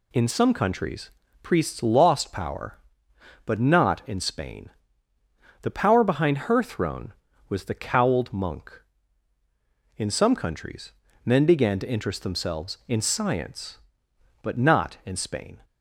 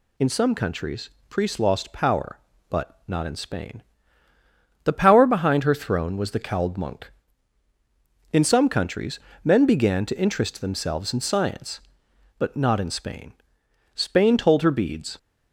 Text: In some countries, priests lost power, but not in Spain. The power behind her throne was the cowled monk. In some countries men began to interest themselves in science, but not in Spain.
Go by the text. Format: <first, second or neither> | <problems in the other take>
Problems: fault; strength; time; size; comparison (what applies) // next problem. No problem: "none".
first | pauses between "countries" and "men"; slight; at 9.1 s; 0.24 s long; slight in the first // goes on to say "Spain told her beads"; noticeable; from 13.9 s on; 1.2 s long